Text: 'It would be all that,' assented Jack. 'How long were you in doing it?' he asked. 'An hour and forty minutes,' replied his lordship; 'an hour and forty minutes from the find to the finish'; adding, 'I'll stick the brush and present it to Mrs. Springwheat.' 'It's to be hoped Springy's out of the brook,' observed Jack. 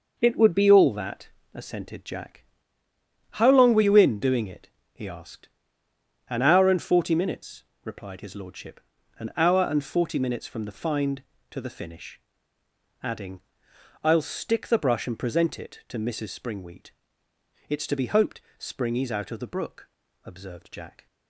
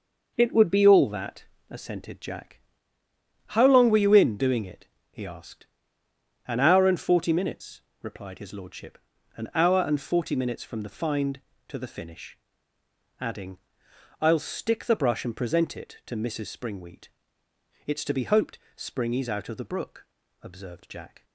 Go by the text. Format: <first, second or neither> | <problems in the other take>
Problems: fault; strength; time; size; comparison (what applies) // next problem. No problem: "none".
neither | pauses between "hoped" and "Springy's"; slight; the same in both